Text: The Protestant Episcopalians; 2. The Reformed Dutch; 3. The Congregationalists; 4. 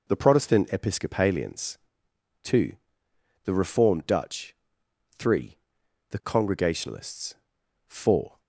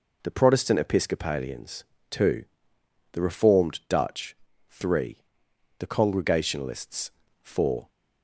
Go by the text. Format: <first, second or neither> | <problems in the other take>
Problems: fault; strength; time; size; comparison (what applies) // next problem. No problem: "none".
neither | none